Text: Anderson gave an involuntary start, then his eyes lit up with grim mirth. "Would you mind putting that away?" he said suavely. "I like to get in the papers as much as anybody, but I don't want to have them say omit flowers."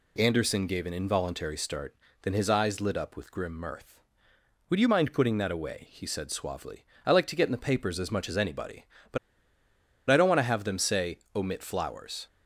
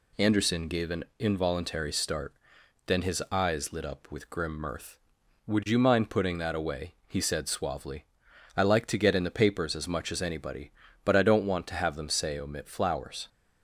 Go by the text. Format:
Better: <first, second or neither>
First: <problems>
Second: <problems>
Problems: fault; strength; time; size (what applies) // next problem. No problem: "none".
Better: second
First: pauses between "but" and "I"; noticeable; at 9.1 s; 0.92 s long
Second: none